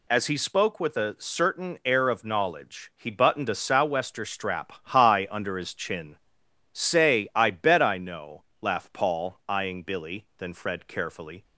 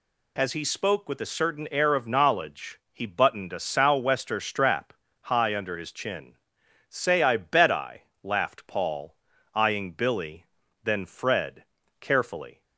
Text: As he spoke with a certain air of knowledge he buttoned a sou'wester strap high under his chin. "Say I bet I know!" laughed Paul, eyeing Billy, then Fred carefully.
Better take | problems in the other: first | pauses between "strap" and "high"; slight; at 4.9 s; 0.28 s long // skips "know"; at 8.1 s // pauses between "Fred" and "carefully"; slight; at 11.6 s; 0.36 s long

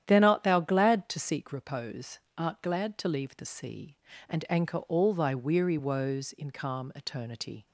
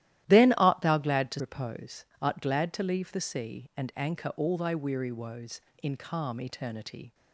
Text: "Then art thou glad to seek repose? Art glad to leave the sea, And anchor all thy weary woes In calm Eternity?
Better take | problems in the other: first | starts louder than the rest; strong; until 1.2 s; 13.5 dB; strong in the first // skips "seek"; at 1.3 s

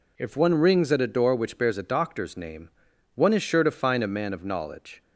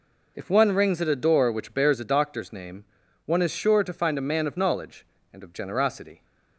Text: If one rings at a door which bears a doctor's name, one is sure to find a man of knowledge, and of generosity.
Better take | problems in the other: second | stops before "and of generosity"; at 5.0 s

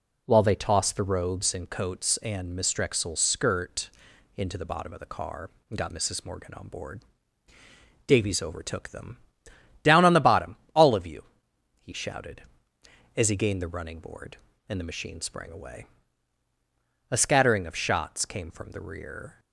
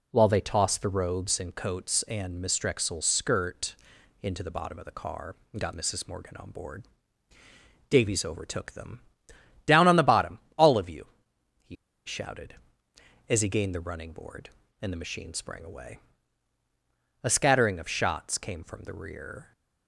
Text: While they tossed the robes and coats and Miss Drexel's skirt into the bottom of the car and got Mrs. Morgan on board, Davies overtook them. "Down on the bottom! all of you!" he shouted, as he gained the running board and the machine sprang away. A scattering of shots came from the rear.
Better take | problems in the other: first | pauses between "skirt" and "into"; noticeable; at 3.7 s; 0.46 s long; noticeable in the first // pauses between "he" and "shouted"; slight; at 11.7 s; 0.30 s long

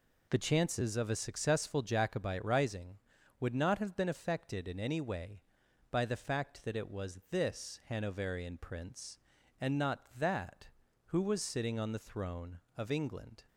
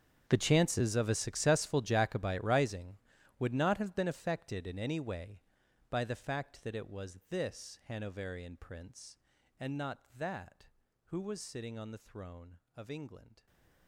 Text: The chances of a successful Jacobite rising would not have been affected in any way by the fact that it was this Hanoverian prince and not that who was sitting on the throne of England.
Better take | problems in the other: first | gets quieter; strong; throughout; 19 dB

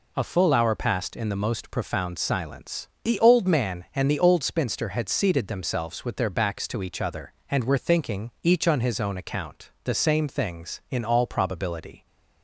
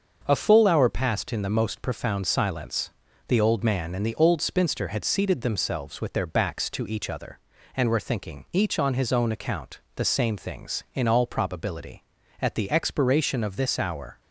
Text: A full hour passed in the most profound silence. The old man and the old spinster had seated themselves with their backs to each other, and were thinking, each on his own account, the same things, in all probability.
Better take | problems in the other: first | starts louder than the rest; until 1.2 s; 6.5 dB // goes on to say "At the expiration of this hour"; strong; from 12.4 s on; 1.8 s long

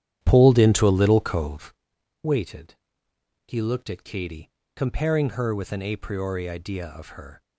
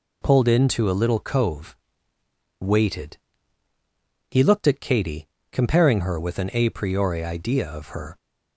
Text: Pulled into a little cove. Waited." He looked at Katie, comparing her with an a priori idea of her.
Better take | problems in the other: second | starts louder than the rest; strong; until 1.8 s; 10.5 dB

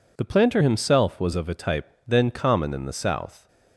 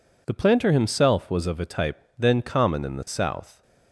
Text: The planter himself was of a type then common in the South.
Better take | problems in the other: neither | pauses between "type" and "then"; slight; the same in both

